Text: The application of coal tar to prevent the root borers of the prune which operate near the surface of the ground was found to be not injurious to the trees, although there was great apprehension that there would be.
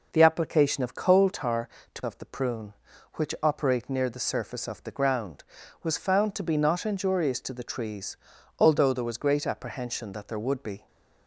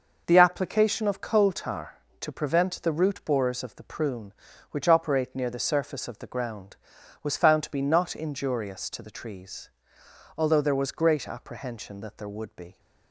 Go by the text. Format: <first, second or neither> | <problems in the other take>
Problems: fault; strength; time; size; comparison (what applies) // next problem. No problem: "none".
second | skips "prevent the root borers"; at 2.0 s